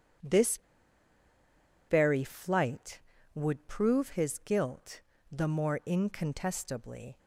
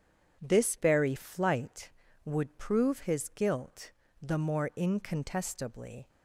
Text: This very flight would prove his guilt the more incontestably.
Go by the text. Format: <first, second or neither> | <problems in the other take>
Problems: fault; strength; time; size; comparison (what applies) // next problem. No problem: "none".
second | pauses between "This" and "very"; strong; at 0.5 s; 1.3 s long // pauses between "guilt" and "the"; slight; at 5.0 s; 0.28 s long; slight in the second